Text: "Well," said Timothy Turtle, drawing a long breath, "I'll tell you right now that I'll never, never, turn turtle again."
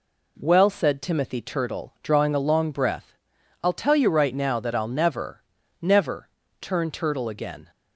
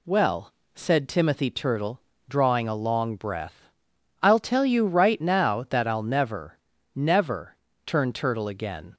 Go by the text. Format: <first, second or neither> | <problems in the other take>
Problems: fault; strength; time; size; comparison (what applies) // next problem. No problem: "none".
neither | none